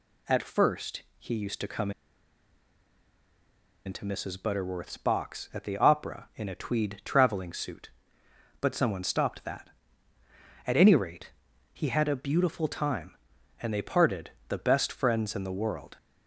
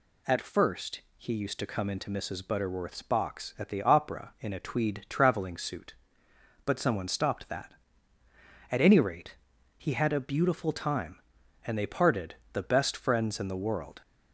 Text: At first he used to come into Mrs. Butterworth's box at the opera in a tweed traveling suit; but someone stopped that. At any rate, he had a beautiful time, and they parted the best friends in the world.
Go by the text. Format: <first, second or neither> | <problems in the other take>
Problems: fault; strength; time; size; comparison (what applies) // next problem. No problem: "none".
second | pauses between "first" and "he"; slight; at 1.0 s; 0.16 s long; slight in the second // pauses between "come" and "into"; strong; at 1.9 s; 1.9 s long // pauses between "parted" and "the"; slight; at 14.3 s; 0.18 s long; slight in the second